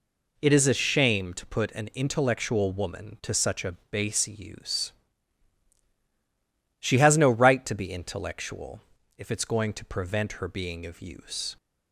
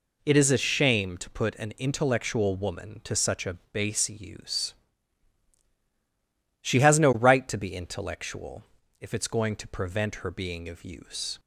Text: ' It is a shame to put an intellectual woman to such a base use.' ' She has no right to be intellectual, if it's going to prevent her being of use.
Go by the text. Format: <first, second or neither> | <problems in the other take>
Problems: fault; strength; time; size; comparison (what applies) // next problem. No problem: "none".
neither | pauses between "a" and "base"; slight; the same in both